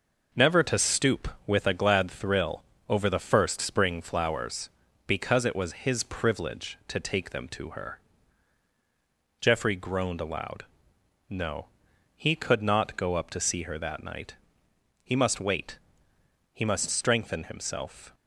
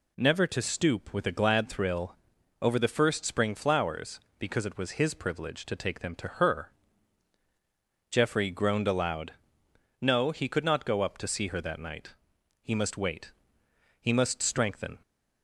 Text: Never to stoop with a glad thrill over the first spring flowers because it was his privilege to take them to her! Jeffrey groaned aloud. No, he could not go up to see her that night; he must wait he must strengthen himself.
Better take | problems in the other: first | pauses between "thrill" and "over"; noticeable; at 2.1 s; 0.46 s long; slight in the first // pauses between "wait" and "he"; noticeable; at 13.3 s; 0.66 s long; noticeable in the first // stops before "himself"; at 15.0 s

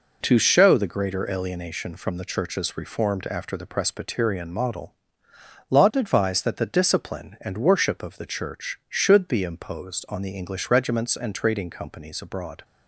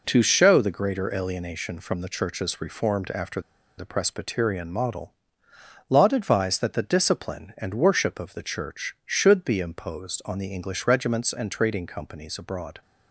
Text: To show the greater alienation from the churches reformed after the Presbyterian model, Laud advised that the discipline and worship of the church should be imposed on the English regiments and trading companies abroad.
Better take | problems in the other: first | pauses between "after" and "the"; at 3.4 s; 0.36 s long

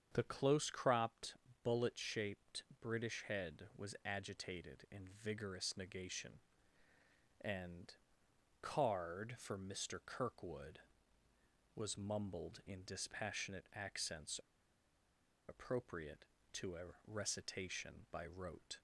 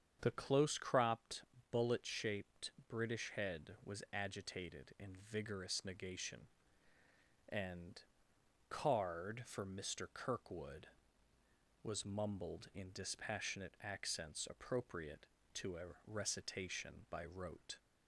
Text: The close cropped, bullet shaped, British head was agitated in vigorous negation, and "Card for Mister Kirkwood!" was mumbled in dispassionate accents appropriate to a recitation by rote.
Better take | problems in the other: second | starts louder than the rest; strong; until 1.1 s; 7.5 dB; strong in the second // pauses between "and" and "Card"; noticeable; at 7.9 s; 0.66 s long; noticeable in the second // pauses between "accents" and "appropriate"; at 14.3 s; 1.1 s long

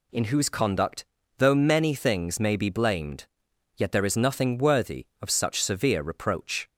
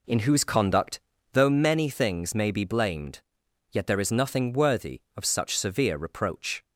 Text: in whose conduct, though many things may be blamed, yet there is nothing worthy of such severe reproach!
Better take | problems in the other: first | starts louder than the rest; slight; until 1.5 s; 3.5 dB

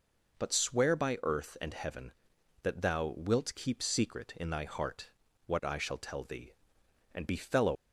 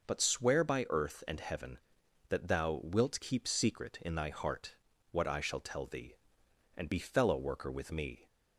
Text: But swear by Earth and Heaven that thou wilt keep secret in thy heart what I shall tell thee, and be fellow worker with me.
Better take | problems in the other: second | pauses between "heart" and "what"; slight; at 5.1 s; 0.36 s long; slight in the second // stops before "worker with me"; at 7.7 s

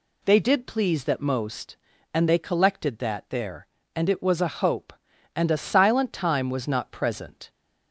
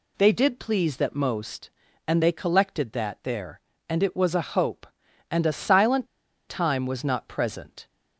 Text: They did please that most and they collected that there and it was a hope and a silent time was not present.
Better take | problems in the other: first | pauses between "silent" and "time"; at 6.0 s; 0.41 s long

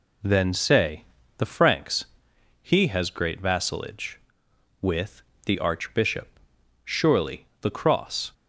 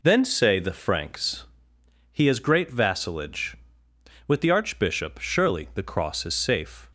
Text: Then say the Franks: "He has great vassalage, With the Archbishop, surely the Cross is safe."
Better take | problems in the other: second | pauses between "say" and "the"; slight; at 1.0 s; 0.34 s long // pauses between "With" and "the"; slight; at 5.2 s; 0.24 s long // stops before "is safe"; at 8.3 s

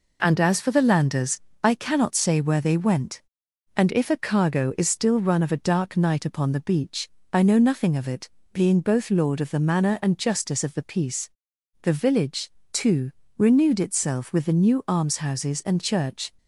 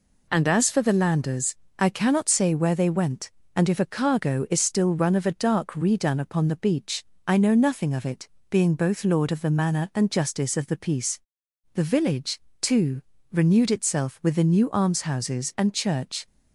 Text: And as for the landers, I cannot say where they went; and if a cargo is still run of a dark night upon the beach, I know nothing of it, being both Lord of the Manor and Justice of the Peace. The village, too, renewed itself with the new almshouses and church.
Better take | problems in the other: first | says "redone" for "night"; at 5.7 s

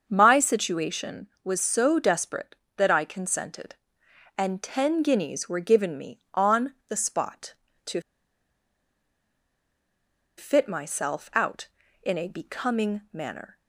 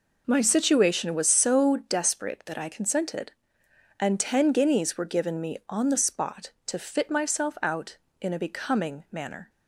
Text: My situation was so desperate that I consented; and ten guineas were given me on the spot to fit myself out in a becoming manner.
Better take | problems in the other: second | starts louder than the rest; until 1.0 s; 6.5 dB // pauses between "to" and "fit"; strong; at 8.0 s; 2.3 s long

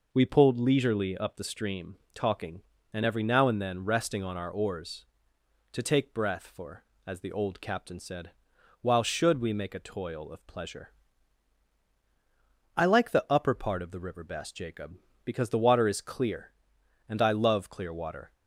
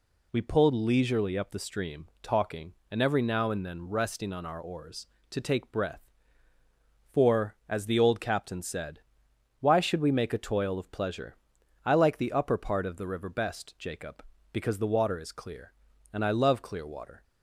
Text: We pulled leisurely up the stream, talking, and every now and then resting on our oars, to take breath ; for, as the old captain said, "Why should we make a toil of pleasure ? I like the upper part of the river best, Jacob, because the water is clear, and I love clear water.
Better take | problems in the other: second | says "While" for "Why"; at 8.8 s

